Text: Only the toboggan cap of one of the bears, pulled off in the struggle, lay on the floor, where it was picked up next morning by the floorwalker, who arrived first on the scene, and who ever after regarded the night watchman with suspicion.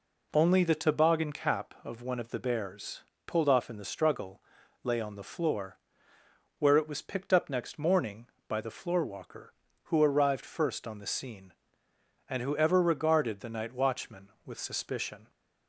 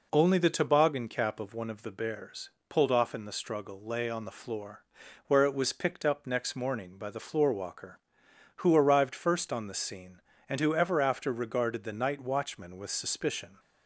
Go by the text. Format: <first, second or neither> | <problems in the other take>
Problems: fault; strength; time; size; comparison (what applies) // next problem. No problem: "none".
second | skips "after"; at 12.7 s